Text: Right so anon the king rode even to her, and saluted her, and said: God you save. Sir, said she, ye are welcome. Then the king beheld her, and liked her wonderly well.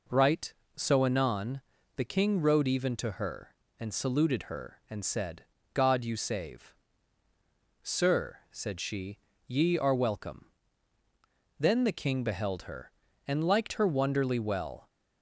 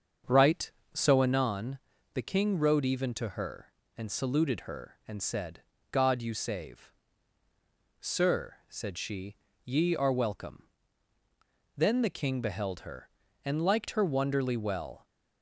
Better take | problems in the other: first | starts louder than the rest; until 1.4 s; 7 dB // pauses between "anon" and "the"; at 1.7 s; 0.38 s long; also in the first

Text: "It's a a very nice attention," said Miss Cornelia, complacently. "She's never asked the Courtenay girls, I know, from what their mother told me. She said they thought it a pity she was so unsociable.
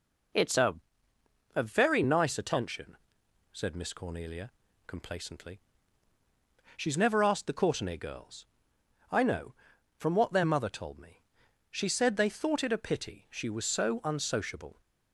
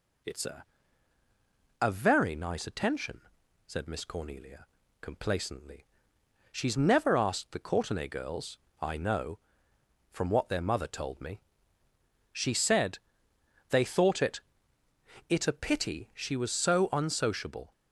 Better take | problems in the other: first | pauses between "a" and "a"; at 0.6 s; 1.1 s long; noticeable in the first // pauses between "said" and "they"; noticeable; at 12.9 s; 0.72 s long // says "it" twice; at 15.2 s

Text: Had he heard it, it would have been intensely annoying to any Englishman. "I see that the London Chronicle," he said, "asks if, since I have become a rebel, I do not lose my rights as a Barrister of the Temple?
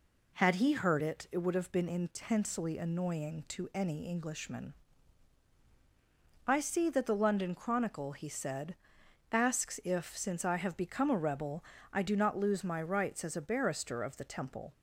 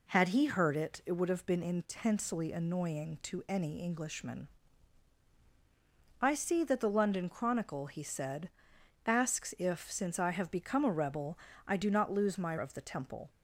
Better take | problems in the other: first | skips "rights as a Barrister"; at 12.5 s

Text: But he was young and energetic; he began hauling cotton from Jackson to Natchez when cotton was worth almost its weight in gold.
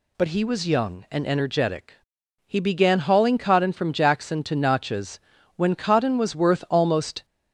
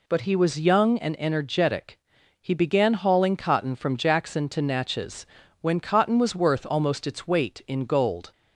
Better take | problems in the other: second | pauses between "Natchez" and "when"; at 5.1 s; 0.38 s long; slight in the second // stops before "its weight in gold"; at 7.2 s

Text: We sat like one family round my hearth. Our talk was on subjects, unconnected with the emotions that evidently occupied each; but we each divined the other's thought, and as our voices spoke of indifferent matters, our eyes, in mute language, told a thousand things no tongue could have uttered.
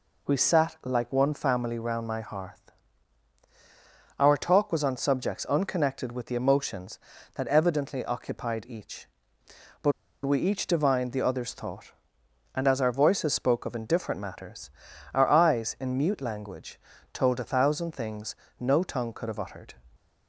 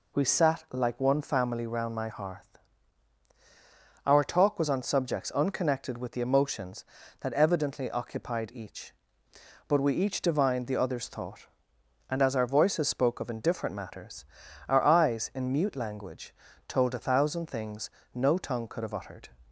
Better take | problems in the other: second | pauses between "but" and "we"; slight; at 9.9 s; 0.33 s long // pauses between "things" and "no"; slight; at 18.3 s; 0.26 s long; slight in the second

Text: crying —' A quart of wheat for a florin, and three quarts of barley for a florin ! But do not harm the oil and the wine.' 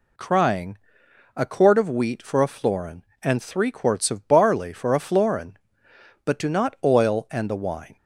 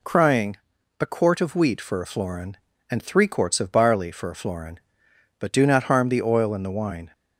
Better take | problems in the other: second | skips "harm the"; at 6.7 s

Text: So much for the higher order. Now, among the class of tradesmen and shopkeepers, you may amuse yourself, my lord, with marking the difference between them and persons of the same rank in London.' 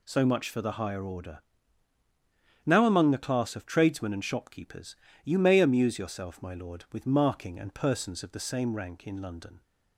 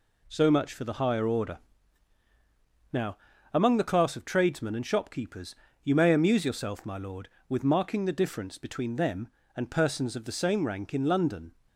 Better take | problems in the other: second | skips "the difference between them"; at 7.5 s

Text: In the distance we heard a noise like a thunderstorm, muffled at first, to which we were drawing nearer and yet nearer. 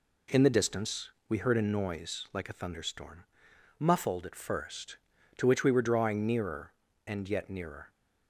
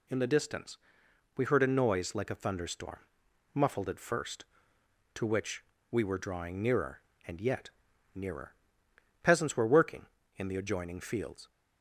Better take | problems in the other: first | pauses between "distance" and "we"; noticeable; at 0.7 s; 0.58 s long; slight in the first // pauses between "which" and "we"; slight; at 5.6 s; 0.28 s long // pauses between "yet" and "nearer"; noticeable; at 7.6 s; 0.46 s long // goes on to say "Peasants were working in the adjoining fields"; strong; from 9.2 s on; 2.2 s long

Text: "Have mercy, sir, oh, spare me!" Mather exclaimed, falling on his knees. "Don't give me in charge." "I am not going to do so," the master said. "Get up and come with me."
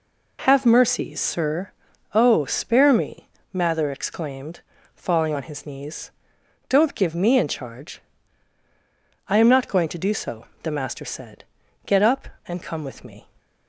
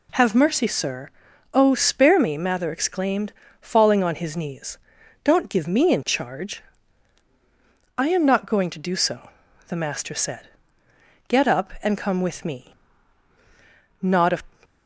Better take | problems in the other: first | goes on to say "Not a"; slight; from 14.0 s on; 0.40 s long

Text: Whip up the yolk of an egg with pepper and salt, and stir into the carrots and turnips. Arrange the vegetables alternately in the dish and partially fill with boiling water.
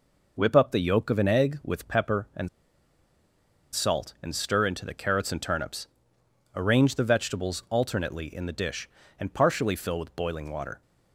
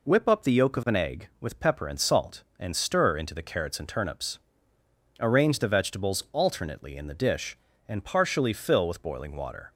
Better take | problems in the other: second | pauses between "and" and "salt"; strong; at 2.4 s; 1.2 s long

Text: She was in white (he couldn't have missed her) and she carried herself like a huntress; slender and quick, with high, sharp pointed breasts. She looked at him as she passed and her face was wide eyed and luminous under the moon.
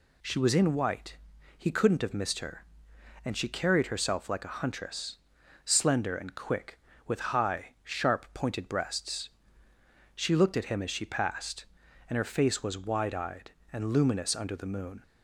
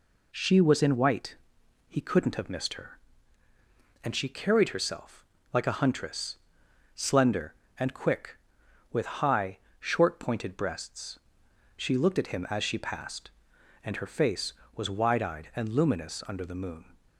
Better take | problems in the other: first | pauses between "herself" and "like"; slight; at 5.2 s; 0.26 s long // says "short" for "sharp"; at 9.7 s

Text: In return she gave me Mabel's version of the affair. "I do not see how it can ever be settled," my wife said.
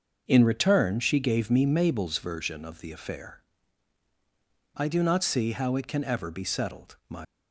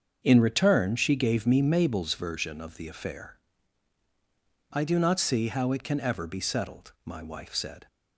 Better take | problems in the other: second | starts louder than the rest; until 1.2 s; 6 dB; also in the second // stops before "wife said"; at 7.2 s

